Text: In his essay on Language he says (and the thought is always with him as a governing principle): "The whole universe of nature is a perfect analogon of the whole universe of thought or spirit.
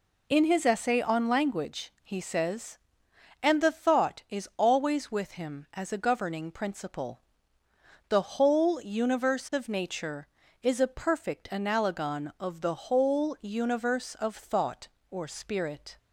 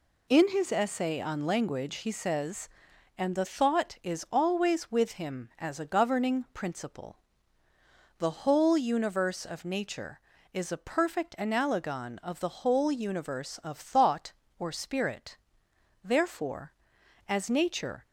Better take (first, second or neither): first